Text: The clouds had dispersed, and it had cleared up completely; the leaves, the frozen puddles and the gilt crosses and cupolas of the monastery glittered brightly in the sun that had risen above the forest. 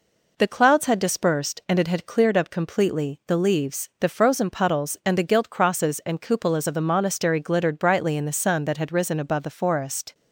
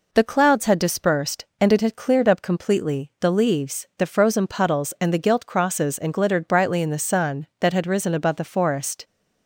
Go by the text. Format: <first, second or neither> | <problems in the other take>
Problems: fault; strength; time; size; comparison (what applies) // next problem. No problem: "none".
first | skips "cupolas of the monastery"; at 6.1 s